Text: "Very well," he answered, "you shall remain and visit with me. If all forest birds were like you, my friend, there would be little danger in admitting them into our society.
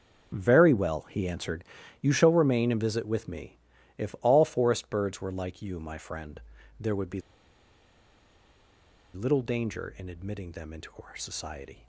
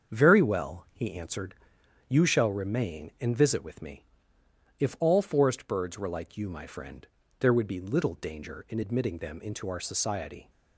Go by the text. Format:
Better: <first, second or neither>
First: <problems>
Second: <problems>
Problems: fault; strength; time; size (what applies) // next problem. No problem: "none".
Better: second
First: starts louder than the rest; until 1.4 s; 6.5 dB // pauses between "be" and "little"; strong; at 7.1 s; 1.9 s long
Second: starts louder than the rest; until 1.1 s; 7 dB